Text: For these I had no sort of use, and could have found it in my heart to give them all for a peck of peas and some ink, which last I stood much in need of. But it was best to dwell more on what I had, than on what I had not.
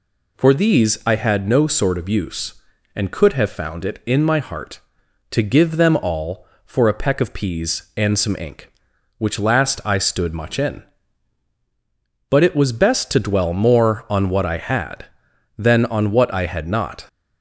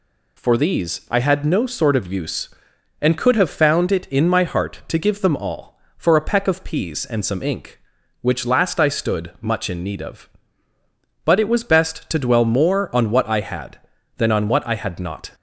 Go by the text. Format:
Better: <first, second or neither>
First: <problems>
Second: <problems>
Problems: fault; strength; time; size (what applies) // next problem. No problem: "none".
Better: second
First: skips "need of"; at 11.5 s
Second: none